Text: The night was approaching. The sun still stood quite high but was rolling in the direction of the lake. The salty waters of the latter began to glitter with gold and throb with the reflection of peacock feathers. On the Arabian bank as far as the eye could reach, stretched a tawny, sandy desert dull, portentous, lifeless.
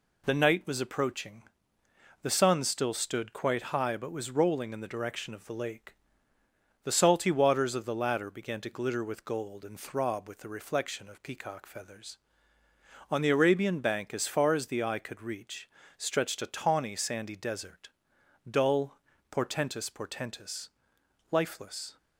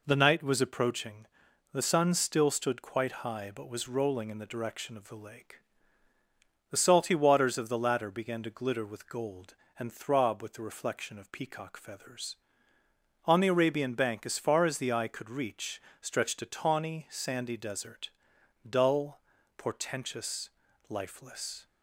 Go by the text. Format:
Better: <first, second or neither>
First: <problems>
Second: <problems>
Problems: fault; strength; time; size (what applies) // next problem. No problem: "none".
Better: second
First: pauses between "desert" and "dull"; noticeable; at 17.8 s; 0.60 s long // says "portentous" twice; at 19.9 s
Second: pauses between "desert" and "dull"; noticeable; at 18.0 s; 0.60 s long